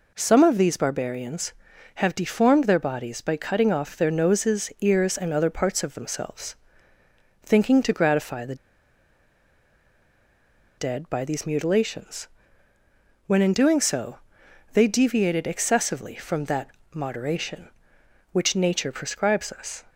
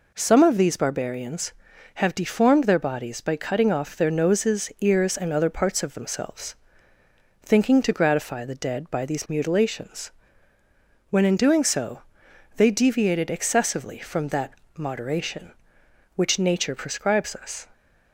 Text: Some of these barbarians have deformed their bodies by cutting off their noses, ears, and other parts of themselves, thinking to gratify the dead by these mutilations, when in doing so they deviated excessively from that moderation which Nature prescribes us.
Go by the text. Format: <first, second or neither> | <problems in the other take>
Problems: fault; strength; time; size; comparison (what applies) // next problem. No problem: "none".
second | pauses between "the" and "dead"; strong; at 8.5 s; 2.2 s long // pauses between "so" and "they"; noticeable; at 14.1 s; 0.54 s long; noticeable in the second // pauses between "that" and "moderation"; slight; at 16.6 s; 0.24 s long; slight in the second